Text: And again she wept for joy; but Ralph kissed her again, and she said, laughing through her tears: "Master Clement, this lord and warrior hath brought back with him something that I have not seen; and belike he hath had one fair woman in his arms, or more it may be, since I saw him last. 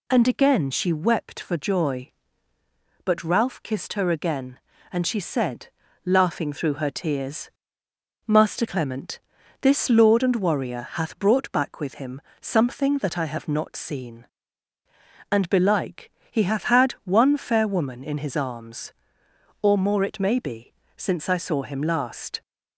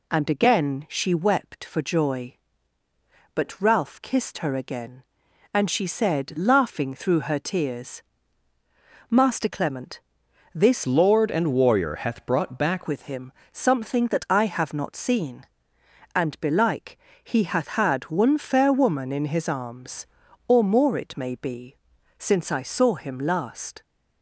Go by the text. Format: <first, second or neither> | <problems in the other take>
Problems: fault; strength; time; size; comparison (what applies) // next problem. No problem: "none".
first | changes voice from "lord" to "back"; from 10.8 to 12.8 s; 2.0 s long // pauses between "him" and "something"; slight; at 13.3 s; 0.22 s long; slight in the first // pauses between "belike" and "he"; slight; at 16.9 s; 0.26 s long; slight in the first